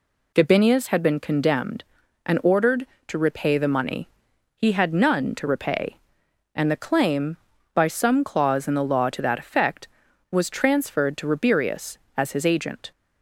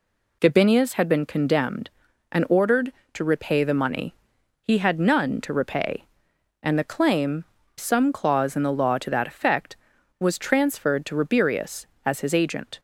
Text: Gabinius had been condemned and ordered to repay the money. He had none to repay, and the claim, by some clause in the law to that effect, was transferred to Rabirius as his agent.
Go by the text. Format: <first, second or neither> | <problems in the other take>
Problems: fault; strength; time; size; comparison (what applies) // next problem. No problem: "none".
first | skips "by"; at 7.6 s